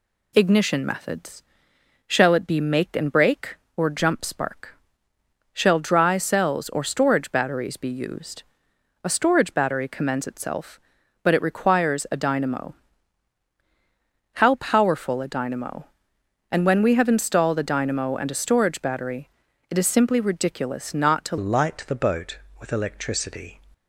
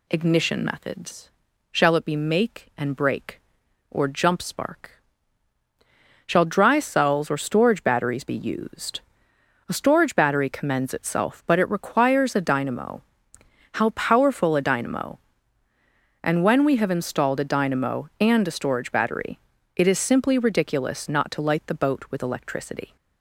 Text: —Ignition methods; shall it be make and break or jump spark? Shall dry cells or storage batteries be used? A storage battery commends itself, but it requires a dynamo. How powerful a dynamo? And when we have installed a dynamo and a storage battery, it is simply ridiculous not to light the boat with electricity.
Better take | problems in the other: second | changes voice at "light"; from 21.3 s on; 2.3 s long

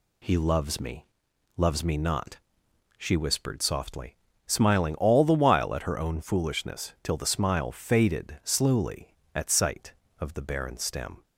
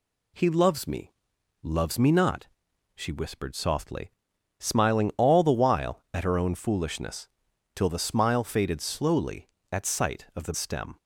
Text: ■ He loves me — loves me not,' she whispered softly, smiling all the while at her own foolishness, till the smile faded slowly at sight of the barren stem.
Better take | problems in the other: first | skips "barren"; at 10.5 s

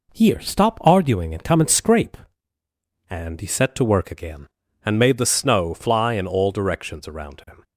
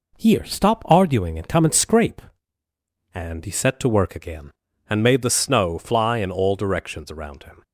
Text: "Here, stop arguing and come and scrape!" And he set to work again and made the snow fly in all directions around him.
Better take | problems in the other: neither | none

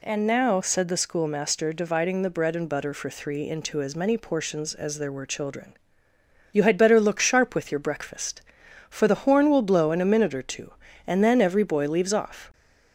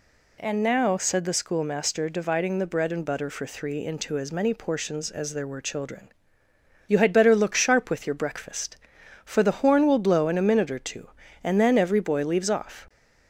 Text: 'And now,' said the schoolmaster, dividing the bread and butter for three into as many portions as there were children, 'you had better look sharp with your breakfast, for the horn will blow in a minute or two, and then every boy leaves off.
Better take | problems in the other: neither | none

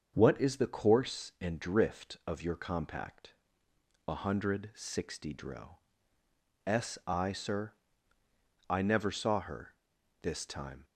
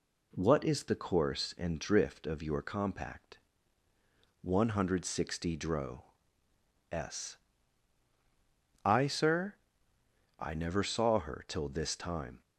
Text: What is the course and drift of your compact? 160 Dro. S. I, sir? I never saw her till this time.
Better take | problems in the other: second | starts louder than the rest; until 1.1 s; 6.5 dB // skips "till"; at 9.9 s

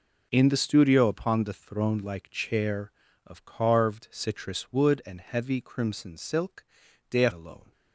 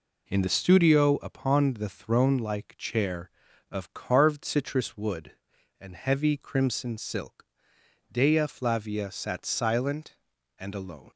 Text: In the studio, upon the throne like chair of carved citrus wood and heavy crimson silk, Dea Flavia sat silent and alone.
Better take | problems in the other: second | skips "Flavia sat silent and"; at 7.3 s

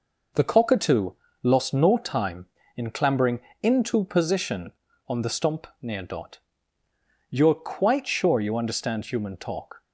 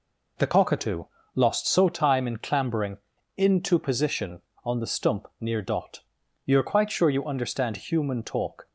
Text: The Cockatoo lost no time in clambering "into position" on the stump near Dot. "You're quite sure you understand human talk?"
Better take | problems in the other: first | pauses between "Cockatoo" and "lost"; slight; at 1.0 s; 0.30 s long; slight in the first // says "so" for "no"; at 1.6 s // pauses between "clambering" and "into"; at 2.9 s; 0.40 s long; slight in the first

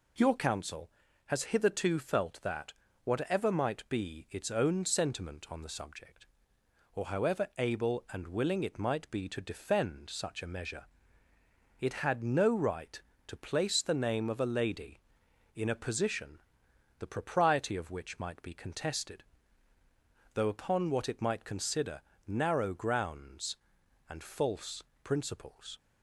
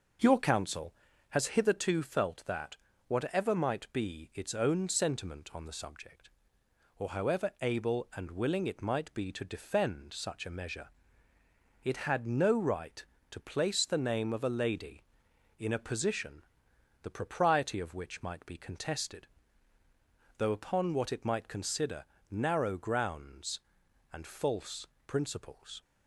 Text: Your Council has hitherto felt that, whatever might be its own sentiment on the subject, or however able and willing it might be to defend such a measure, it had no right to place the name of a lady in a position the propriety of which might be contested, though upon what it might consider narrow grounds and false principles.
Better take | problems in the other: first | starts louder than the rest; noticeable; until 1.7 s; 6 dB // pauses between "position" and "the"; noticeable; at 16.4 s; 0.60 s long; noticeable in the first // pauses between "consider" and "narrow"; slight; at 22.0 s; 0.26 s long; slight in the first // pauses between "false" and "principles"; slight; at 24.8 s; 0.22 s long; slight in the first

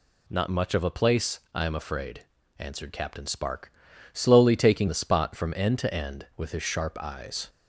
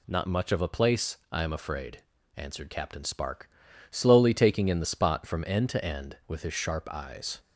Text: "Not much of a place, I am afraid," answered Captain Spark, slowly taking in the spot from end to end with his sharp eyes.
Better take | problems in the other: second | skips "in"; at 4.8 s

